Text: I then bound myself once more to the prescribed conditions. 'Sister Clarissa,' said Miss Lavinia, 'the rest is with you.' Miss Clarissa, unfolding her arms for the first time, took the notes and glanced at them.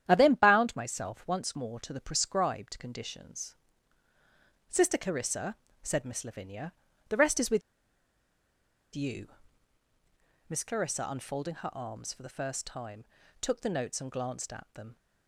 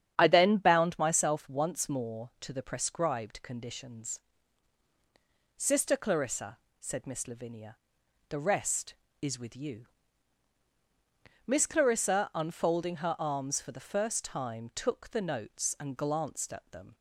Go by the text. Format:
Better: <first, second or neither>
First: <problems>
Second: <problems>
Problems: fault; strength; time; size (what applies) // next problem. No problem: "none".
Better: second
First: starts louder than the rest; strong; until 1.0 s; 10 dB // pauses between "with" and "you"; strong; at 7.6 s; 1.3 s long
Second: starts louder than the rest; strong; until 1.1 s; 9 dB